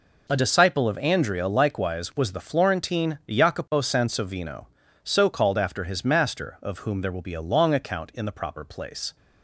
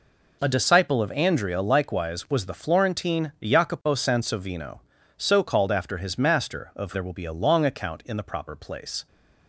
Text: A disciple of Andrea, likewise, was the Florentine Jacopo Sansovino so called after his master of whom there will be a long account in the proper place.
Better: first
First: none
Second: skips "whom"; at 6.9 s

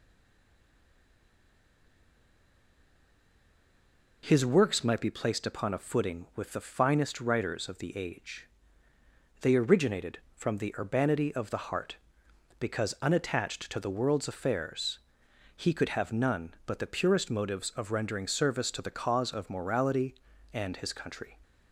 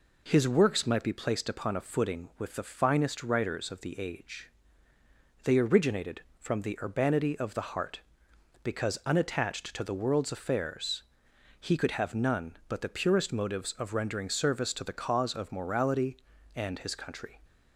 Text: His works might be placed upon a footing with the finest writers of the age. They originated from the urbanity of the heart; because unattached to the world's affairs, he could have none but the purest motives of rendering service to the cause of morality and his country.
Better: second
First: stays silent before the first word; strong; until 4.2 s; 4.2 s long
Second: none

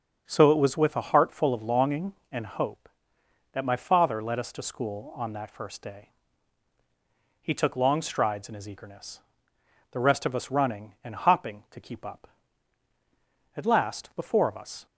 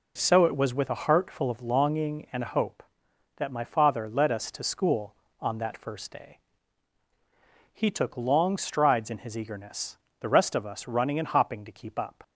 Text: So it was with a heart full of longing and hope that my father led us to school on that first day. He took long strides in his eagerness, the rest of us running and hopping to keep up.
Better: second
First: starts louder than the rest; strong; until 1.2 s; 7 dB // goes on to say "At last the four of us"; noticeable; from 13.5 s on; 1.3 s long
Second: none

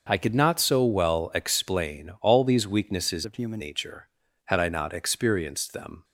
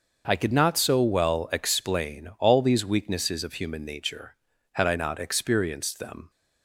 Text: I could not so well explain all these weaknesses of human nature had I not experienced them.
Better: second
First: starts louder than the rest; until 1.1 s; 6 dB // changes voice from "of" to "human"; from 3.2 to 3.5 s; 0.3 s long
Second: starts louder than the rest; until 1.2 s; 6 dB

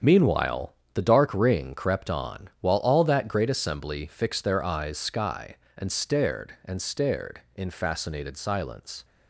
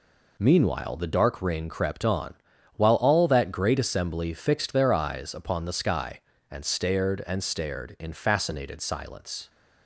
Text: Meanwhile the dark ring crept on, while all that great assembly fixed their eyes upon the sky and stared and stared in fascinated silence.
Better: second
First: starts louder than the rest; strong; until 1.2 s; 7.5 dB // pauses between "Meanwhile" and "the"; slight; at 0.7 s; 0.20 s long // skips "upon the"; at 4.9 s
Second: none

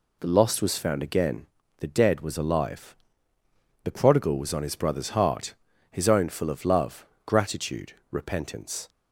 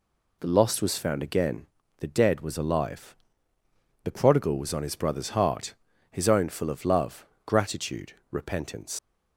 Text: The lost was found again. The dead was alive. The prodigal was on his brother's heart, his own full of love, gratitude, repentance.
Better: first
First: none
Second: leaves "repentance" unfinished; at 8.9 s; 100 ms

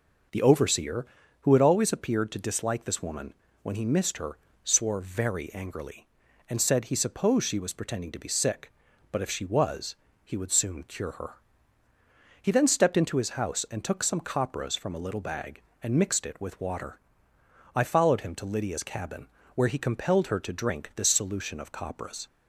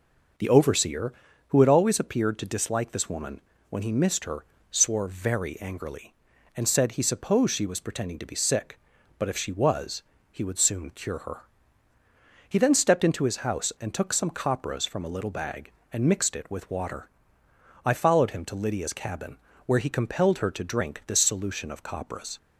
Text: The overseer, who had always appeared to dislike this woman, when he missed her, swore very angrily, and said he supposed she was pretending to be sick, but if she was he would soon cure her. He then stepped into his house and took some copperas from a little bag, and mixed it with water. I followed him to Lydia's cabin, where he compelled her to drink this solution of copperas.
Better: neither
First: pauses between "was" and "he"; slight; at 9.9 s; 0.28 s long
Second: pauses between "was" and "he"; slight; at 10.0 s; 0.28 s long

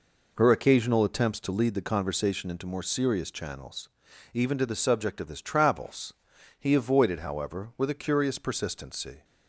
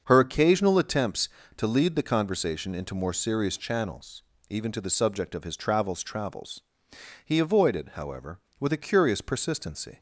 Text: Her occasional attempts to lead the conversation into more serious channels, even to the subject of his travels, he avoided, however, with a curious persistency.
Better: first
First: none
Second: starts louder than the rest; until 1.0 s; 6.5 dB // says "travels" twice; at 6.0 s

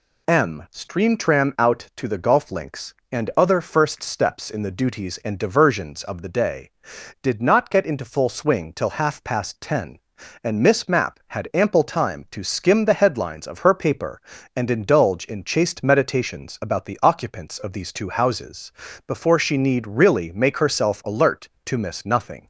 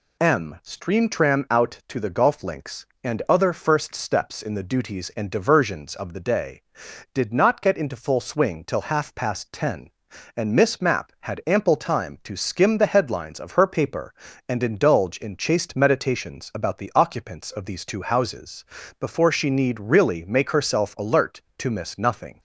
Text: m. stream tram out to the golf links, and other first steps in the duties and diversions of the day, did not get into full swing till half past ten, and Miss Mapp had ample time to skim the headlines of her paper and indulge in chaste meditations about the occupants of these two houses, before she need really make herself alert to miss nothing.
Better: neither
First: none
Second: none

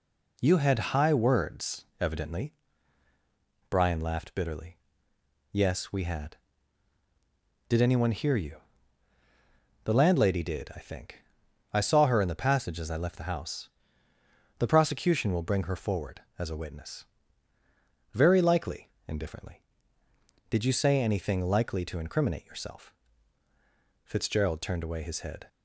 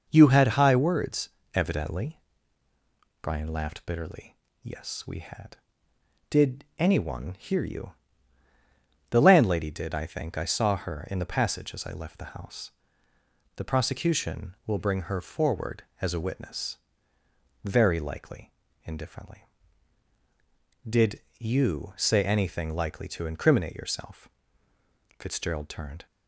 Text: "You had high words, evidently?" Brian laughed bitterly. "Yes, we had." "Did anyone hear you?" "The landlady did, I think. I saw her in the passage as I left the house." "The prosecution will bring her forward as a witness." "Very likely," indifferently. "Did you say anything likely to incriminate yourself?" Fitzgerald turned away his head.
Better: first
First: none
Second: pauses between "Did" and "you"; slight; at 21.1 s; 0.18 s long // stops before "away his head"; at 26.0 s

